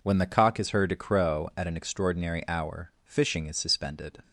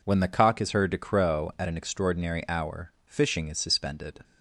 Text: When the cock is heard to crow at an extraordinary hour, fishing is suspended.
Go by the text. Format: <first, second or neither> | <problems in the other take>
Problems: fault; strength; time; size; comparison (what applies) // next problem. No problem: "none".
neither | none